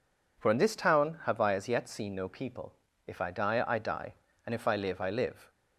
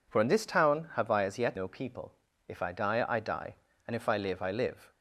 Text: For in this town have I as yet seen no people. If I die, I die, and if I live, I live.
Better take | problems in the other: first | skips "seen"; at 1.5 s

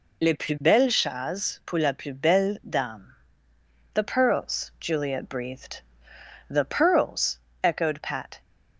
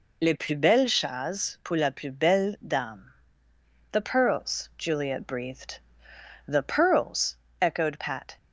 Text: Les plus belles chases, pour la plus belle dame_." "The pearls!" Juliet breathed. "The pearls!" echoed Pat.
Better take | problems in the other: neither | none

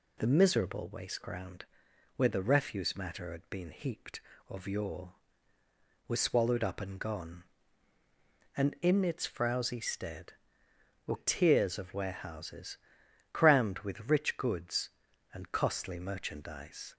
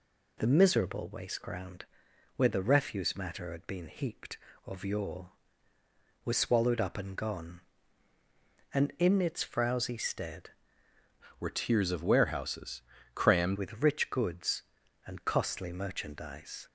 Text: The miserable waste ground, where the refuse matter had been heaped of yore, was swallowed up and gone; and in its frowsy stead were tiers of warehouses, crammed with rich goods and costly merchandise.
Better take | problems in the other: first | changes voice from "were" to "crammed"; from 11.4 to 13.5 s; 2.1 s long

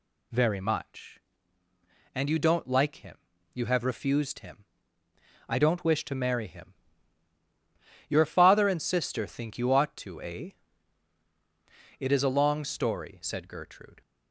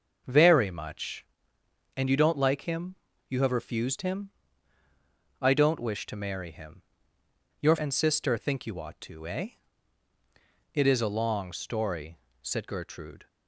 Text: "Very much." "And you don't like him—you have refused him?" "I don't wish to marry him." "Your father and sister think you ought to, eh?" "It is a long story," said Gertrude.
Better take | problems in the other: first | skips "father"; at 7.7 s

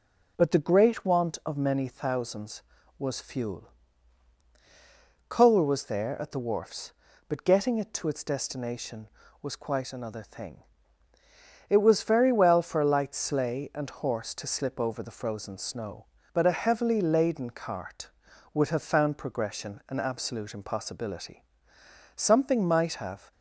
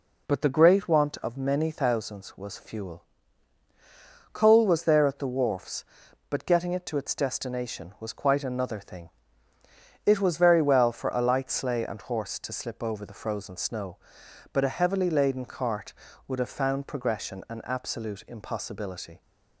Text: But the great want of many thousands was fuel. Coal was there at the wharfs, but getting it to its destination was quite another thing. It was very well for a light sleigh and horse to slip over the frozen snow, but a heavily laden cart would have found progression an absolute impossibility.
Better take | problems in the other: second | goes on to say "Something might have"; noticeable; from 22.1 s on; 1.1 s long

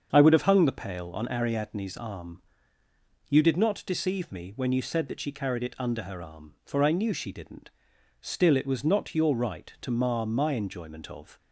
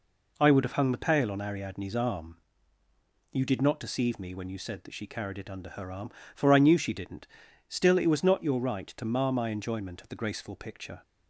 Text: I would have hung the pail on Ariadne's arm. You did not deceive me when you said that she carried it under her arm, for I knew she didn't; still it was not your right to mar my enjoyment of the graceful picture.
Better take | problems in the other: second | starts louder than the rest; until 1.1 s; 7 dB // stops before "the graceful picture"; at 11.3 s

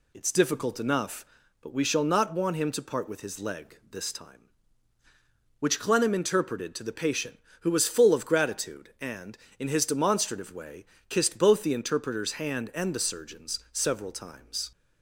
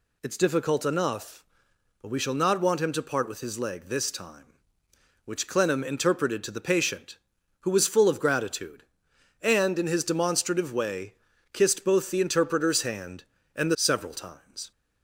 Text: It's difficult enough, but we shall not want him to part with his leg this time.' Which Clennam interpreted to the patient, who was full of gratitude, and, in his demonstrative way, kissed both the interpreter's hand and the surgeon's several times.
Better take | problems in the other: first | skips "surgeon's"; at 13.7 s

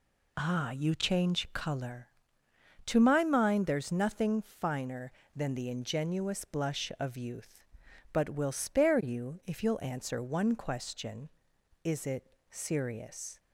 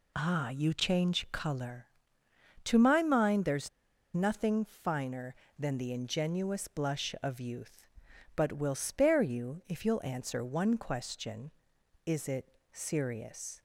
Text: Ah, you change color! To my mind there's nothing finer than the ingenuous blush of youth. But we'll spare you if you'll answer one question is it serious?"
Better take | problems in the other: first | pauses between "there's" and "nothing"; noticeable; at 3.6 s; 0.46 s long // pauses between "it" and "serious"; slight; at 12.4 s; 0.22 s long; slight in the first

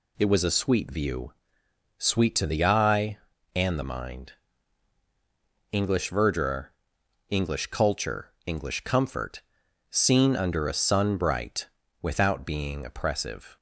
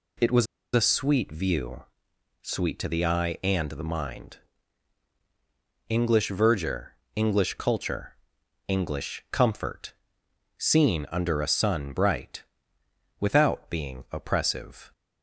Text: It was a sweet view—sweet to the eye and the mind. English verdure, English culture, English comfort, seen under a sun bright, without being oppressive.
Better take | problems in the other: first | pauses between "was" and "a"; slight; at 0.4 s; 0.30 s long

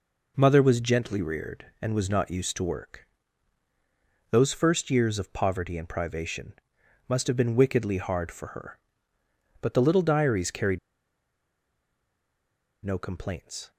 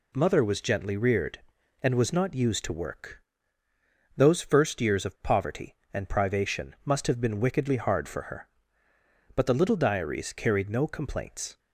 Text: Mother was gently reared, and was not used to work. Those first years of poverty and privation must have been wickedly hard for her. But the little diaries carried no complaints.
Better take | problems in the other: second | pauses between "privation" and "must"; noticeable; at 6.5 s; 0.54 s long // pauses between "carried" and "no"; strong; at 10.7 s; 2.0 s long

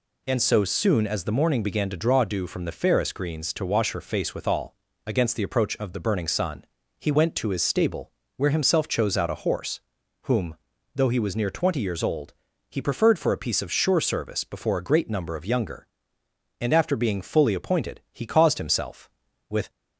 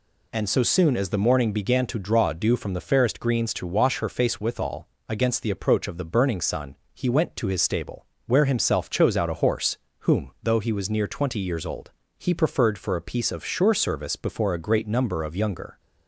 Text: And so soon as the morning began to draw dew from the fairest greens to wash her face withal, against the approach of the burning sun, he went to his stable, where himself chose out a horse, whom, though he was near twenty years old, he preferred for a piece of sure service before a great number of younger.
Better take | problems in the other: second | goes on to say "And after being fully appointed he caused himself with"; strong; from 16.5 s on; 3.1 s long

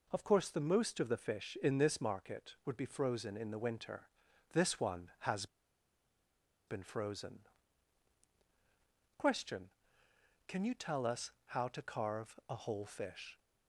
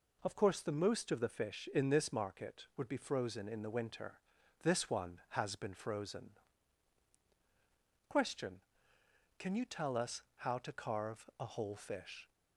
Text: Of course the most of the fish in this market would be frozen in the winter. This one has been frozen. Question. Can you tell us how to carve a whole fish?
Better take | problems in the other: second | pauses between "has" and "been"; at 5.4 s; 1.2 s long

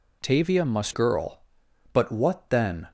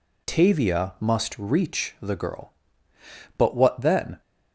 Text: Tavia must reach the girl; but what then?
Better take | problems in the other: second | skips "reach the"; at 0.9 s

